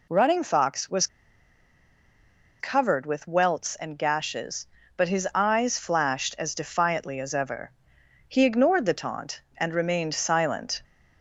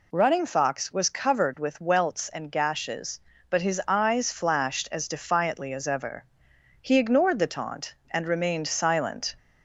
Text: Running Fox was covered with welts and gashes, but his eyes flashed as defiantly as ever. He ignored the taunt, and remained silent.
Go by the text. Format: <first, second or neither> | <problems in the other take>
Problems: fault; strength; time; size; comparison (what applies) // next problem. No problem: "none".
second | pauses between "was" and "covered"; strong; at 1.0 s; 1.5 s long